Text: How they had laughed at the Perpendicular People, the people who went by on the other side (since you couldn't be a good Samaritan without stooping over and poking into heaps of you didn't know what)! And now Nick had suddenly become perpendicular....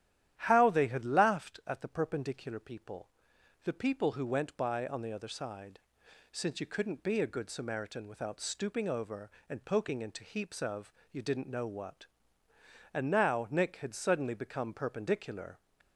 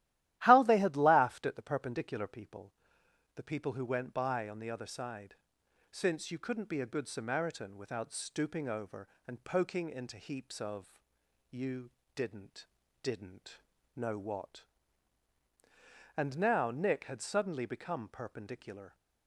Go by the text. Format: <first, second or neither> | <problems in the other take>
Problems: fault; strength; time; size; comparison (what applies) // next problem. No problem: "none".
first | starts louder than the rest; strong; until 1.4 s; 14 dB; strong in the first // pauses between "of" and "you"; noticeable; at 10.9 s; 0.58 s long; slight in the first // pauses between "you" and "didn't"; slight; at 11.9 s; 0.24 s long // says "didn't" twice; at 13.0 s